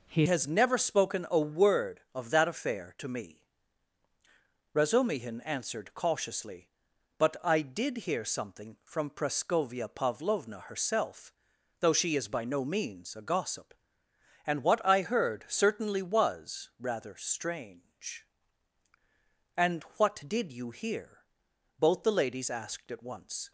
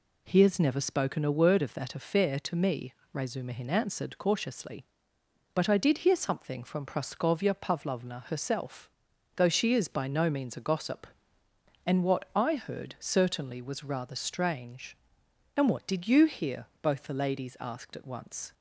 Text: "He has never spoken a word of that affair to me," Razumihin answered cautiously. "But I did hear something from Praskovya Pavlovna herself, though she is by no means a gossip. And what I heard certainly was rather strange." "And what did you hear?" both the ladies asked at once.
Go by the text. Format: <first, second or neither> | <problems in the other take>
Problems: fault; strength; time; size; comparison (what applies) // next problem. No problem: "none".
second | changes voice at "has"; from 0.2 s on; 23.3 s long